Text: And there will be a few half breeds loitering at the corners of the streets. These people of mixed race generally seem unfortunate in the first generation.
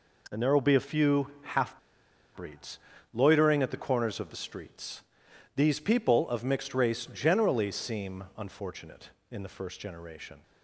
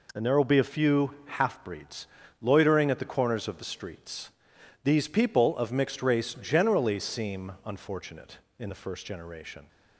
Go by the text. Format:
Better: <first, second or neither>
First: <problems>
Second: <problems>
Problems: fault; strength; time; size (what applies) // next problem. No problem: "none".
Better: second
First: pauses between "half" and "breeds"; noticeable; at 1.7 s; 0.56 s long // pauses between "breeds" and "loitering"; slight; at 2.7 s; 0.34 s long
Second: pauses between "breeds" and "loitering"; slight; at 2.0 s; 0.34 s long